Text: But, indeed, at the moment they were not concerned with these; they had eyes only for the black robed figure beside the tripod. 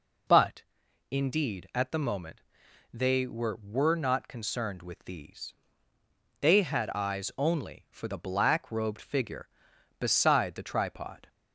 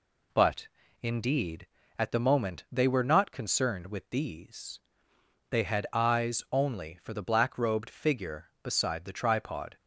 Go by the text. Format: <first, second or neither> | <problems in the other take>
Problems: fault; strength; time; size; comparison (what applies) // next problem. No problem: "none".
second | pauses between "moment" and "they"; noticeable; at 2.4 s; 0.50 s long // says "were" twice; at 3.5 s